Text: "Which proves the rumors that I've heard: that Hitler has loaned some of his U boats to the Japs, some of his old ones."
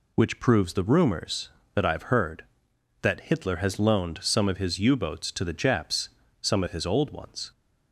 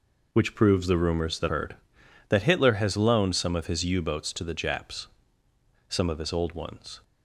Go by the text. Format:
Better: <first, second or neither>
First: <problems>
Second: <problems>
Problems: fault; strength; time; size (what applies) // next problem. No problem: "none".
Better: first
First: none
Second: skips "I've"; at 1.4 s